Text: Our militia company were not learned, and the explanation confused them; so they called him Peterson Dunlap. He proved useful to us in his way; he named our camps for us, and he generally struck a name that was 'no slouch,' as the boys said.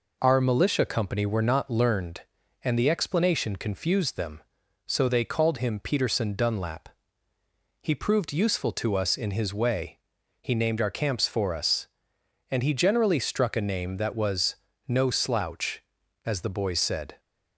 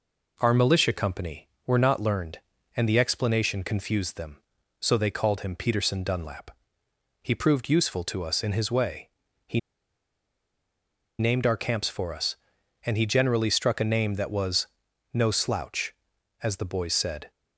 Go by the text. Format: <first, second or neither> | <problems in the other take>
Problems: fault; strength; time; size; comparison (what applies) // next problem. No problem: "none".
first | pauses between "he" and "named"; strong; at 9.5 s; 1.5 s long // pauses between "was" and "no"; noticeable; at 14.6 s; 0.48 s long; slight in the first